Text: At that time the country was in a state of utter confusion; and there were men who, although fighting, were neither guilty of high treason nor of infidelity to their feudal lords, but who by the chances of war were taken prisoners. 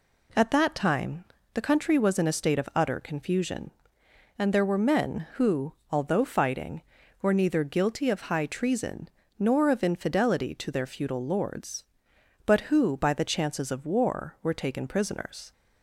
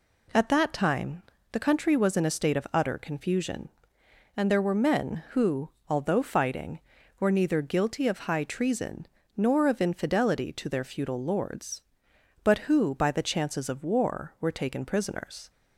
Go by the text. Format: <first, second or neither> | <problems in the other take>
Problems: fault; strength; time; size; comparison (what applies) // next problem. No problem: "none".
neither | pauses between "time" and "the"; slight; the same in both // pauses between "treason" and "nor"; slight; the same in both